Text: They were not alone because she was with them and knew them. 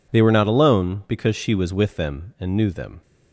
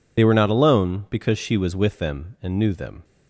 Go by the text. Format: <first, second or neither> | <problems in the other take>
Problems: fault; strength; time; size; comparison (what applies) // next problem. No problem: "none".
first | loses the start of "They"; at 0.1 s; 60 ms